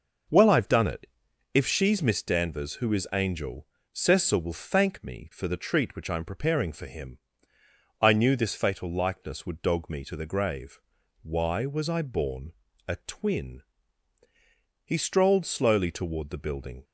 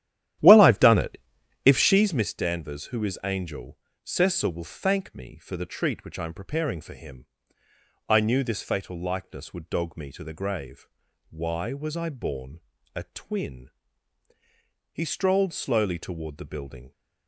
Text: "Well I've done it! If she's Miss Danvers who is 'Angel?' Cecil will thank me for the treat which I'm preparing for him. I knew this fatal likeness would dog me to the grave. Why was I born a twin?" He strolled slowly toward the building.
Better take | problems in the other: first | starts louder than the rest; strong; until 2.2 s; 11.5 dB // pauses between "born" and "a"; slight; at 12.5 s; 0.34 s long; slight in the first

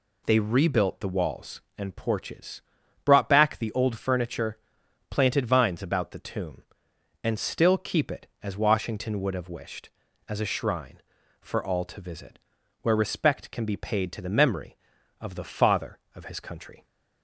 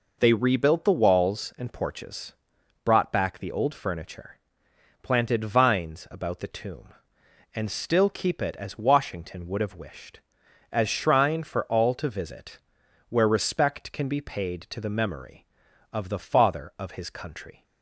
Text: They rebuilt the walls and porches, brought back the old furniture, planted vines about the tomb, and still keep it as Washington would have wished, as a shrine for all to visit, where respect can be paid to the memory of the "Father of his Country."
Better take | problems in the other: first | skips "a"; at 10.8 s

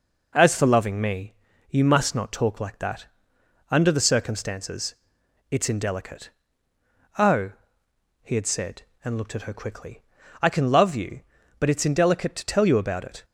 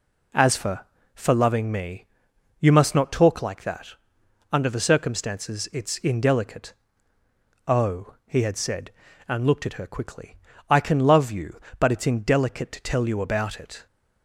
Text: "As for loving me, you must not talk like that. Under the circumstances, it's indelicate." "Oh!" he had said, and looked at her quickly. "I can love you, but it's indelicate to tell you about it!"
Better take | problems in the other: first | says "for" twice; at 1.1 s

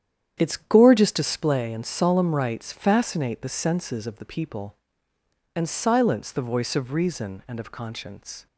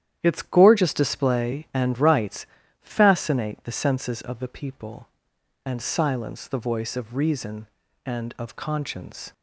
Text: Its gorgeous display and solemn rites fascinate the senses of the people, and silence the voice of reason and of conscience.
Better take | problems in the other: first | starts louder than the rest; strong; until 1.2 s; 10.5 dB; strong in the first // skips "solemn"; at 1.9 s // pauses between "rites" and "fascinate"; slight; at 2.4 s; 0.36 s long

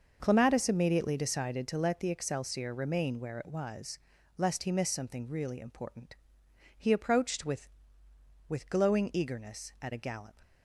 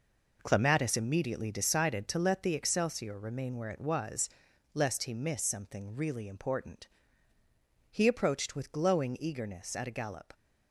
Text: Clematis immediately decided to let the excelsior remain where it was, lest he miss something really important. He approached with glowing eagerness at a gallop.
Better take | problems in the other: second | says "with" twice; at 8.4 s

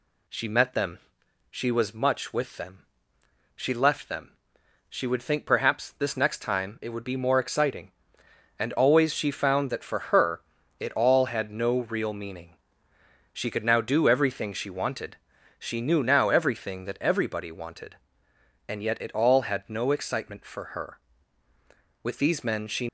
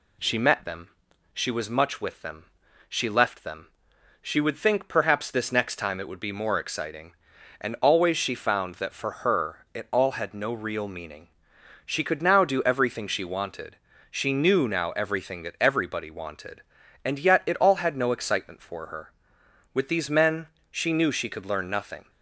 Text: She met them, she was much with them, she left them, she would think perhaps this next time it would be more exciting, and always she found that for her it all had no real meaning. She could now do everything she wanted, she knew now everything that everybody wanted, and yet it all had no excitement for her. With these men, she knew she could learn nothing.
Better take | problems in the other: second | pauses between "her" and "it"; at 10.4 s; 0.38 s long // stops before "knew she could learn nothing"; at 22.8 s

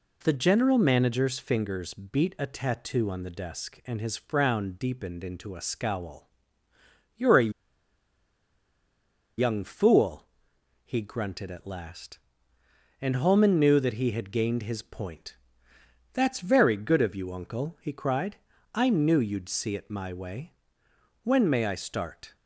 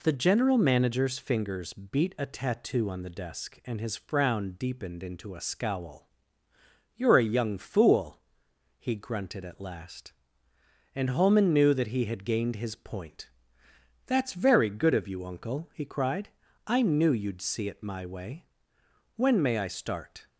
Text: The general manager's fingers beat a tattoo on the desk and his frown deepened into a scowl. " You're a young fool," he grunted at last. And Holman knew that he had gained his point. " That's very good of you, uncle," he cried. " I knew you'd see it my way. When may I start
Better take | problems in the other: second | pauses between "a" and "young"; strong; at 7.5 s; 1.8 s long

